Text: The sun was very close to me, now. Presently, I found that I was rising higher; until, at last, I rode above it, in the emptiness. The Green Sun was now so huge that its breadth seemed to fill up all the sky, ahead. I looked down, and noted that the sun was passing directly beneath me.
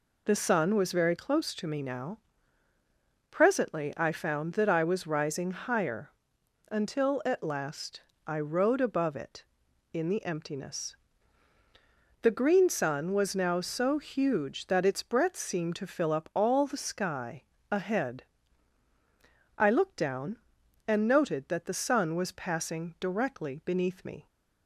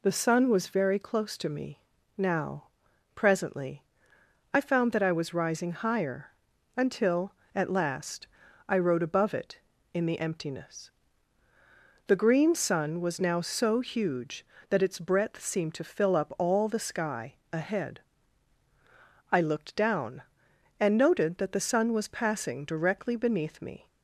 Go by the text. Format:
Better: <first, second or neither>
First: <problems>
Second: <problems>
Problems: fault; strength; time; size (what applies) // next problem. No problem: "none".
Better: neither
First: none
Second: none